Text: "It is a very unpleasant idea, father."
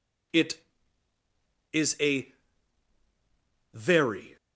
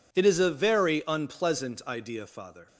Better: second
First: pauses between "a" and "very"; strong; at 2.3 s; 1.4 s long // stops before "unpleasant idea father"; at 4.3 s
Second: none

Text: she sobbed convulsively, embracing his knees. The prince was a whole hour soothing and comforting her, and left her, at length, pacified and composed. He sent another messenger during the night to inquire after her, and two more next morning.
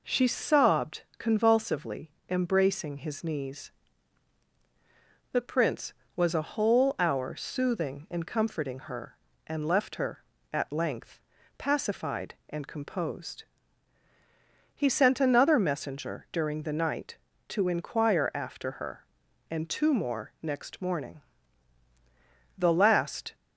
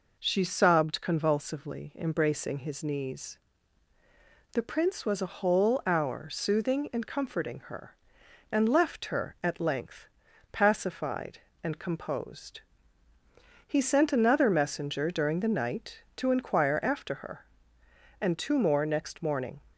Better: second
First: pauses between "sobbed" and "convulsively"; slight; at 1.0 s; 0.16 s long // goes on to say "The last"; noticeable; from 22.5 s on; 0.76 s long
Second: none

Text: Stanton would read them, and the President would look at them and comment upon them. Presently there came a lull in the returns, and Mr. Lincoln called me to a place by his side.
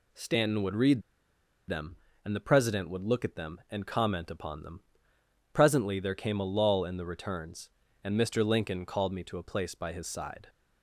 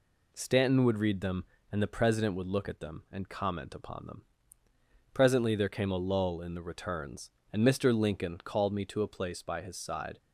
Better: second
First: pauses between "read" and "them"; noticeable; at 1.0 s; 0.67 s long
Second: none

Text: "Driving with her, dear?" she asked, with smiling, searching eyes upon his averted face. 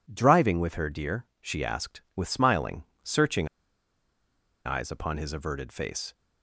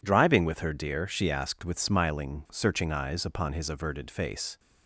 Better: second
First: pauses between "searching" and "eyes"; at 3.4 s; 1.1 s long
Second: none

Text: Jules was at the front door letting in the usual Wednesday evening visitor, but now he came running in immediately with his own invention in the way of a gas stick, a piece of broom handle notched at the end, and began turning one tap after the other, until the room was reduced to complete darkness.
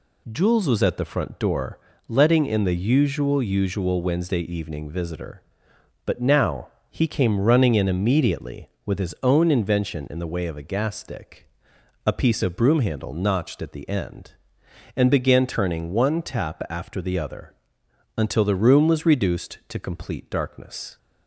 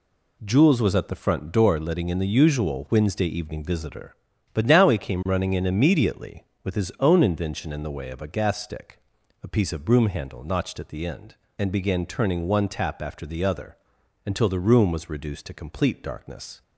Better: second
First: pauses between "door" and "letting"; slight; at 1.7 s; 0.30 s long // says "usual" twice; at 3.4 s // pauses between "now" and "he"; slight; at 6.6 s; 0.22 s long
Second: none

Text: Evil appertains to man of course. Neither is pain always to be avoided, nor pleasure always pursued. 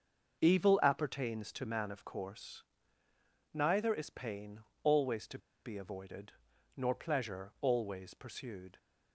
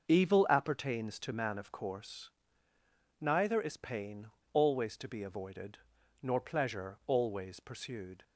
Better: second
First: pauses between "pain" and "always"; slight; at 4.5 s; 0.24 s long // pauses between "to" and "be"; slight; at 5.3 s; 0.25 s long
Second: pauses between "pain" and "always"; slight; at 4.2 s; 0.26 s long

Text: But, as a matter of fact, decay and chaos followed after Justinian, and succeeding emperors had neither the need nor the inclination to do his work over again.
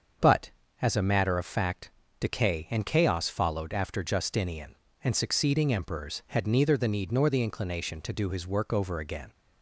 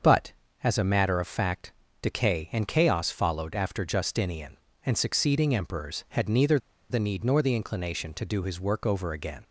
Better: first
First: starts louder than the rest; until 1.5 s; 7 dB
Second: starts louder than the rest; until 1.3 s; 7 dB // pauses between "neither" and "the"; slight; at 6.5 s; 0.32 s long

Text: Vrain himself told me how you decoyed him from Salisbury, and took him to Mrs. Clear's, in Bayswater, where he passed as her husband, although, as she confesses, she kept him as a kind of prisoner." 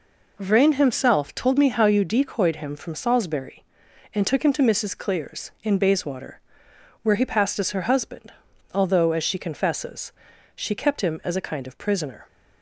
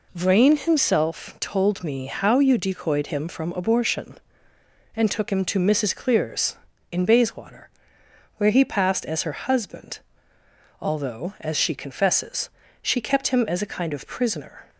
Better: first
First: none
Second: says "Abortion" for "Salisbury"; at 3.5 s

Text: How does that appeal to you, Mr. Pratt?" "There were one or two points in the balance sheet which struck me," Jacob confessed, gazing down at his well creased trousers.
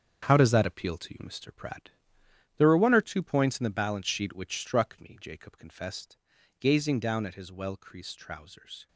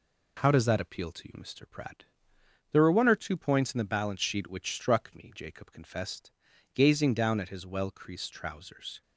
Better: second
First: gets quieter; strong; throughout; 8 dB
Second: none

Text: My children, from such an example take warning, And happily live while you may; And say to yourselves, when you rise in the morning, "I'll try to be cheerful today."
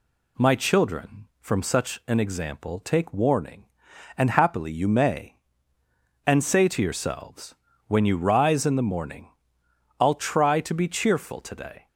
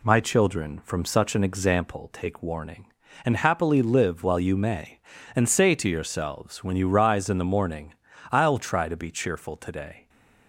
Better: second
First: skips "live while"; at 4.7 s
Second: none

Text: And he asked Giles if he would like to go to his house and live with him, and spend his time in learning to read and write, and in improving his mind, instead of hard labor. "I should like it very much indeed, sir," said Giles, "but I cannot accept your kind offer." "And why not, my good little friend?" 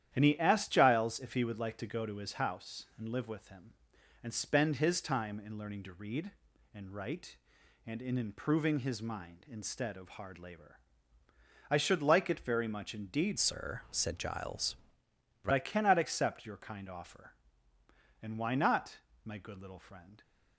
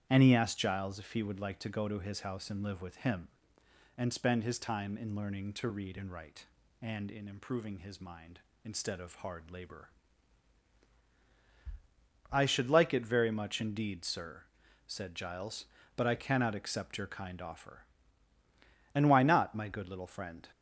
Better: second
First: starts louder than the rest; strong; until 1.1 s; 10.5 dB // changes voice from "sir" to "but"; from 13.3 to 15.5 s; 2.2 s long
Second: starts louder than the rest; strong; until 1.1 s; 10 dB

